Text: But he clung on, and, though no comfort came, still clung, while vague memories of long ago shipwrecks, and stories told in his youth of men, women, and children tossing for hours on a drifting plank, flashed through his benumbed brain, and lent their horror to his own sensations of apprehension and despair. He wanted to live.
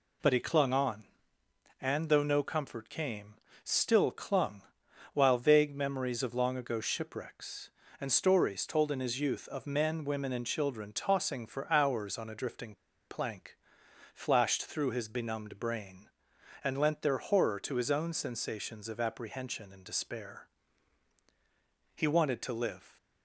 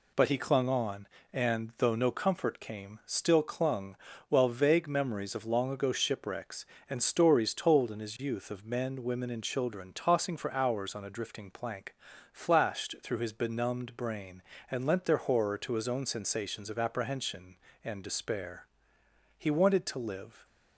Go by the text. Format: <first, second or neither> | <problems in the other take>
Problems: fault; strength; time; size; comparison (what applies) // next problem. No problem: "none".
second | pauses between "drifting" and "plank"; slight; at 12.7 s; 0.33 s long